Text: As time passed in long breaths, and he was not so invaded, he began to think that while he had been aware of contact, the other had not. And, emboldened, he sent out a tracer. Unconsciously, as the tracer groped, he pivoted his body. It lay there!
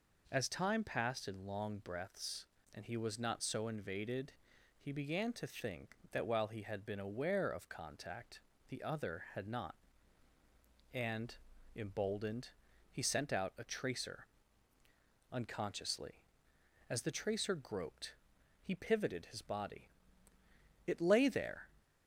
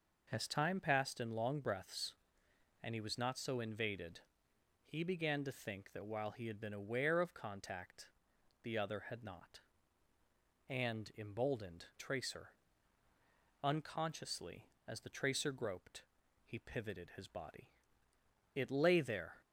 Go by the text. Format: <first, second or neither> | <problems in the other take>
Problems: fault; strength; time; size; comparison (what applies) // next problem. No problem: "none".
first | skips "he sent out a"; at 11.9 s